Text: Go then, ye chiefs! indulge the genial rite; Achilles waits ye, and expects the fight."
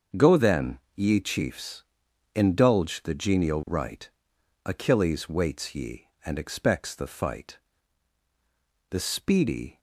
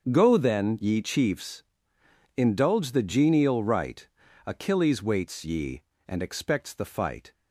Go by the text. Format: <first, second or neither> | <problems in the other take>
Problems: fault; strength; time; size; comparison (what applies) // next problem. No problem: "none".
second | starts louder than the rest; until 1.3 s; 6.5 dB; also in the second // goes on to say "The speedy"; noticeable; from 8.9 s on; 0.88 s long